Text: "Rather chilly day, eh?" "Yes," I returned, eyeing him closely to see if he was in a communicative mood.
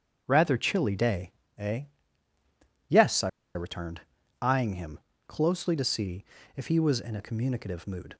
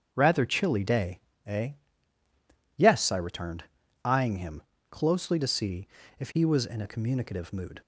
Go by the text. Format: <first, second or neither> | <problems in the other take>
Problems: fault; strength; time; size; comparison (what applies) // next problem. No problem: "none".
second | starts louder than the rest; strong; until 1.2 s; 8 dB; strong in the second // pauses between "I" and "returned"; slight; at 3.2 s; 0.27 s long // pauses between "him" and "closely"; slight; at 4.9 s; 0.30 s long; slight in the second // pauses between "see" and "if"; slight; at 6.2 s; 0.30 s long; slight in the second